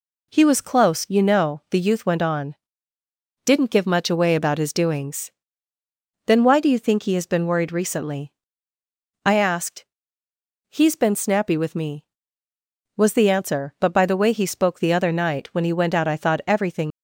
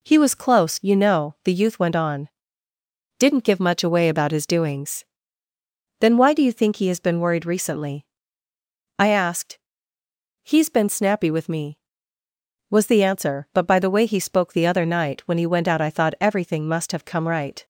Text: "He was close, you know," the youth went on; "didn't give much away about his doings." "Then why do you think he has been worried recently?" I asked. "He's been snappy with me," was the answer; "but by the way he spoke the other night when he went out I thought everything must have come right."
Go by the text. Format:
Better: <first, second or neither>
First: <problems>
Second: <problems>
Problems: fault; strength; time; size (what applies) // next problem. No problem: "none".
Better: second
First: stops before "must have come right"; at 16.9 s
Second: none